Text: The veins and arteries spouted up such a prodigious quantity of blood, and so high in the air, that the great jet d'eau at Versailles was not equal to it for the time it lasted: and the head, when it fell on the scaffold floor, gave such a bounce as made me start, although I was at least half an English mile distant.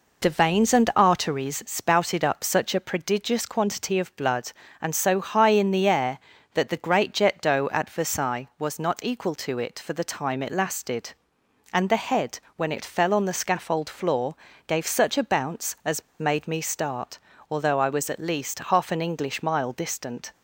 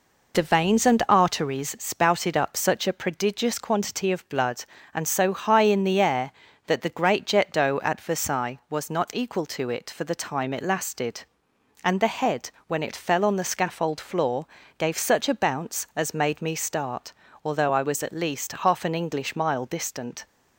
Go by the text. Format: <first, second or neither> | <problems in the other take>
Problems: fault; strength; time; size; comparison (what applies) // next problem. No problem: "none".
second | pauses between "as" and "made"; slight; at 16.0 s; 0.17 s long